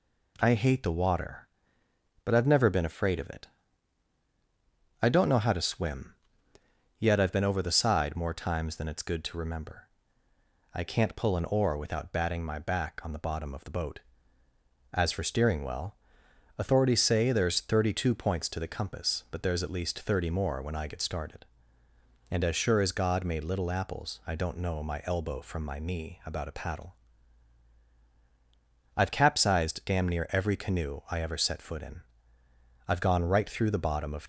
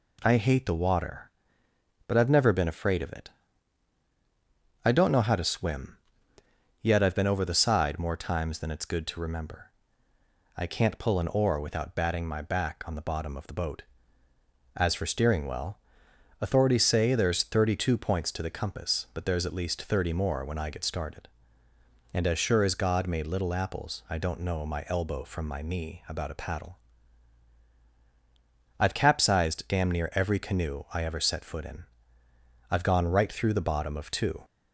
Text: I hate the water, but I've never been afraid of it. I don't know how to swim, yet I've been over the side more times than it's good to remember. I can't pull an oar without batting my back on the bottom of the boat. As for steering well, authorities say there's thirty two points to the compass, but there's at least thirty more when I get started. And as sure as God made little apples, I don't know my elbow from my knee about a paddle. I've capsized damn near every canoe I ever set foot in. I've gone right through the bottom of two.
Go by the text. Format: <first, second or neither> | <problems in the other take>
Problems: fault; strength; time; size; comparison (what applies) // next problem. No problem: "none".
second | stops before "two"; at 34.2 s